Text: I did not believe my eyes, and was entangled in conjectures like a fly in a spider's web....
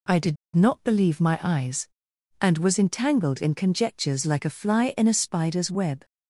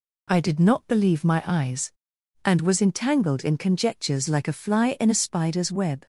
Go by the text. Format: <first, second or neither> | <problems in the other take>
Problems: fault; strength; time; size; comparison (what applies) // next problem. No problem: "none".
second | pauses between "did" and "not"; slight; at 0.3 s; 0.18 s long